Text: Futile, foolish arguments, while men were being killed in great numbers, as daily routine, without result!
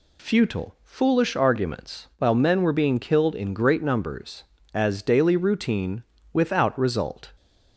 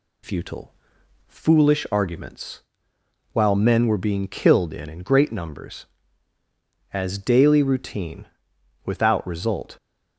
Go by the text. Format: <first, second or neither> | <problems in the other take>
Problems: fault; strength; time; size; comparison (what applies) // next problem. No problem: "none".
first | says "in" twice; at 4.8 s